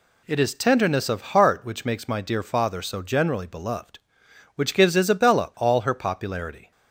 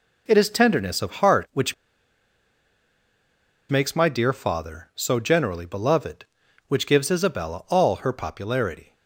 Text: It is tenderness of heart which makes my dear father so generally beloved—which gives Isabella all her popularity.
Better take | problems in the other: first | pauses between "which" and "makes"; strong; at 1.7 s; 1.9 s long

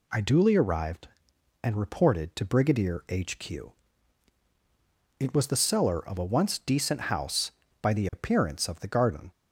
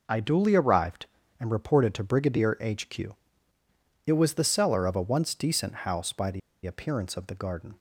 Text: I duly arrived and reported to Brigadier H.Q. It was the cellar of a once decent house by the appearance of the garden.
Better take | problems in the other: first | pauses between "the" and "appearance"; slight; at 6.4 s; 0.25 s long

